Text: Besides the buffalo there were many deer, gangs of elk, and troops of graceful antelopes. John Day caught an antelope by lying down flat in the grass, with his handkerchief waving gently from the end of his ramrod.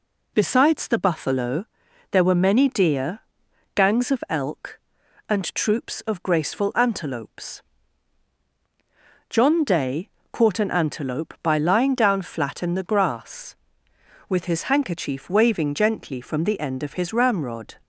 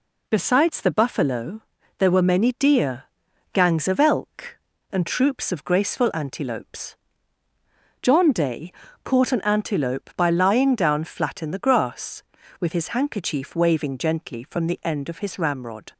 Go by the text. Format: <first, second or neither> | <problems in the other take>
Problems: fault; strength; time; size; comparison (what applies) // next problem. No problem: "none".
neither | pauses between "buffalo" and "there"; the same in both // pauses between "Day" and "caught"; slight; the same in both